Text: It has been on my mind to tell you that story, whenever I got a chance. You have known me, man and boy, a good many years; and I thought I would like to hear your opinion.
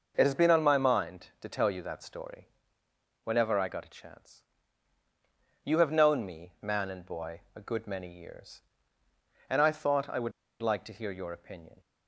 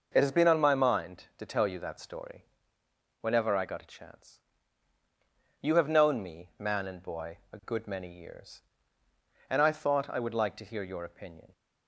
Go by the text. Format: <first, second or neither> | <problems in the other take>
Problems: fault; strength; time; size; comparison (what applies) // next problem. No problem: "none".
second | pauses between "would" and "like"; slight; at 10.3 s; 0.30 s long